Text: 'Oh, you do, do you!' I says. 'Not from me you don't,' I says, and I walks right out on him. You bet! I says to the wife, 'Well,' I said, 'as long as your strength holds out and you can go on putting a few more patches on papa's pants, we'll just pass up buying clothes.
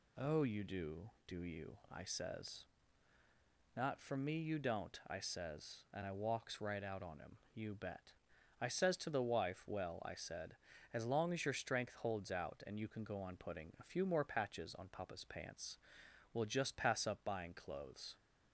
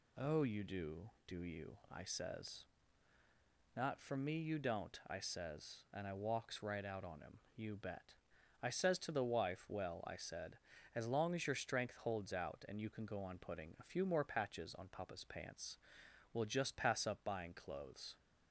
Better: neither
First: none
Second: none

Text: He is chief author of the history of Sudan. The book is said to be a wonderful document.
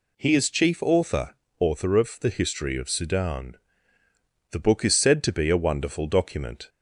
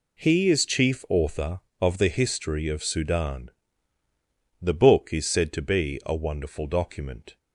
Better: second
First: says "author" twice; at 1.5 s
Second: none

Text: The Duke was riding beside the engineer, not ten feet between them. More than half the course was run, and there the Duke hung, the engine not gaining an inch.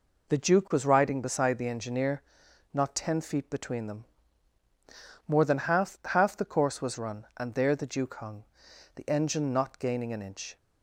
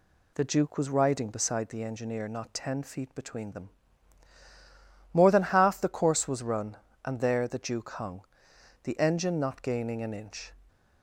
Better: second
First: says "half" twice; at 6.0 s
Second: none

